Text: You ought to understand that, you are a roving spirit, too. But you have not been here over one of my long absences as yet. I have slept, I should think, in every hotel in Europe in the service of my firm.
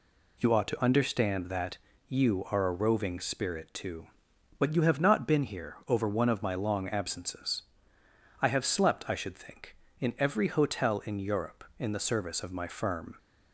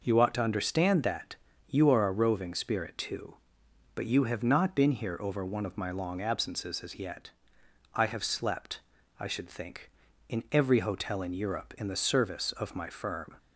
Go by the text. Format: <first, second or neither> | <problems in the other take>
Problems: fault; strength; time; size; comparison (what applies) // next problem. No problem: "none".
second | skips "as yet"; at 8.0 s